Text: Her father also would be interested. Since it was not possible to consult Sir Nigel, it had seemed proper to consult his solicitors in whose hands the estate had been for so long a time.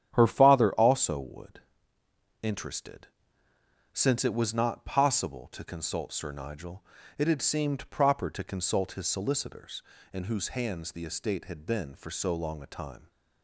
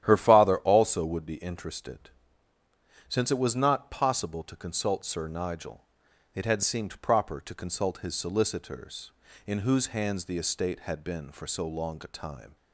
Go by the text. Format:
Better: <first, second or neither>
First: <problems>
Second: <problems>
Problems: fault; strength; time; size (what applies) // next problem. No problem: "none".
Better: second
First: starts louder than the rest; strong; until 1.1 s; 9.5 dB // skips "be"; at 2.0 s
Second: starts louder than the rest; strong; until 1.0 s; 10.5 dB